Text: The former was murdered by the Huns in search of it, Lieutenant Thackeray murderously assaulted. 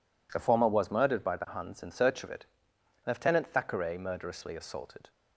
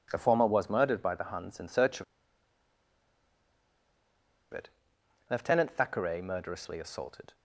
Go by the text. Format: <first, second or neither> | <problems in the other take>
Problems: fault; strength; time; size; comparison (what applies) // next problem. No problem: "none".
first | pauses between "of" and "it"; strong; at 2.0 s; 2.4 s long